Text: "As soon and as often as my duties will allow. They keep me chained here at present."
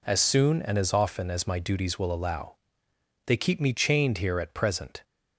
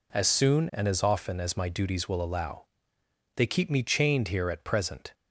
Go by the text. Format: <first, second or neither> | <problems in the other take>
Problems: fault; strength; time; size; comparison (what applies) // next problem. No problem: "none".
neither | none